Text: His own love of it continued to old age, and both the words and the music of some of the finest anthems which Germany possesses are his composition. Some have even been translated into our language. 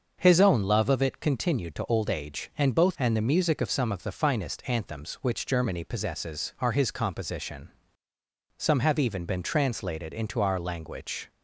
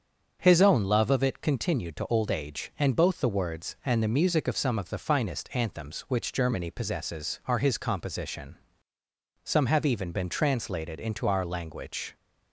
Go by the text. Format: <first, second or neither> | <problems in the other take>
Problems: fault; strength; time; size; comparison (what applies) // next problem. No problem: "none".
second | starts louder than the rest; until 1.1 s; 6.5 dB; also in the second // skips "the words"; at 2.9 s